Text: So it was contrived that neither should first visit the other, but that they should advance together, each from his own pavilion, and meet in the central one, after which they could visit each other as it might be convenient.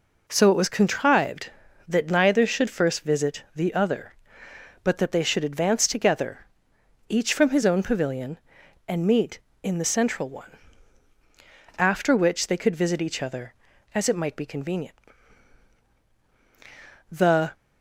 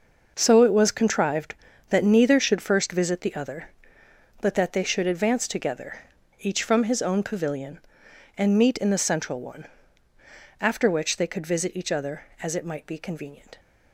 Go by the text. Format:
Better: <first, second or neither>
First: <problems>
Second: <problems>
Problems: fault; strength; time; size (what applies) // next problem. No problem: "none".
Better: second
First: goes on to say "The"; slight; from 17.1 s on; 0.40 s long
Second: none